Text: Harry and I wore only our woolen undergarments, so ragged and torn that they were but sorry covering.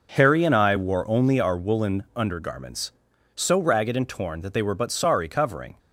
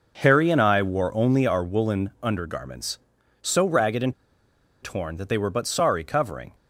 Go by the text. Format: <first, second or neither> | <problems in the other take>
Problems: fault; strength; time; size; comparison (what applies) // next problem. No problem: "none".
first | pauses between "and" and "torn"; noticeable; at 4.1 s; 0.69 s long